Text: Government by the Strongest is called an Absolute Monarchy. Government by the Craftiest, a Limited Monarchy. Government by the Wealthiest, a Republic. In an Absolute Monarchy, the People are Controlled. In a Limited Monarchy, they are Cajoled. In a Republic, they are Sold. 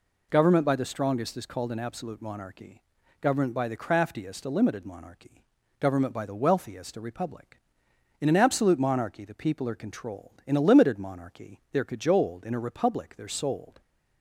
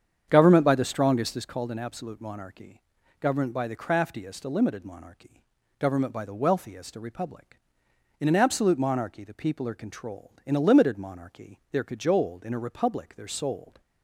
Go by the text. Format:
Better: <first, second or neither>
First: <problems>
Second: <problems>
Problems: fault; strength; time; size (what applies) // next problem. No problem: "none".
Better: first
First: none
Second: starts louder than the rest; strong; until 1.5 s; 8 dB